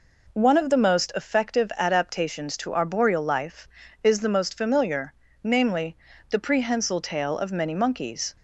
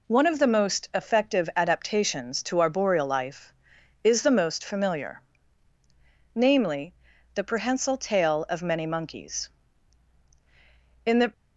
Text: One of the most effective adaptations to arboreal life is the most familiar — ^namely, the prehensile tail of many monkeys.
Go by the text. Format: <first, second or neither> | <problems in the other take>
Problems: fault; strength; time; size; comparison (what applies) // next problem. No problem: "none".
first | goes on to say "In the"; slight; from 11.0 s on; 0.26 s long